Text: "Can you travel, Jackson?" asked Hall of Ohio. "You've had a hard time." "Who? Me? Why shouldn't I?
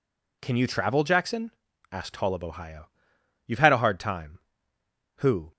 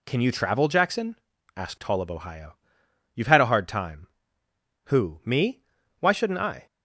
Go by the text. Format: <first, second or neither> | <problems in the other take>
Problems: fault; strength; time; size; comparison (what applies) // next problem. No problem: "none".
second | stops before "Me Why shouldn't I"; at 5.5 s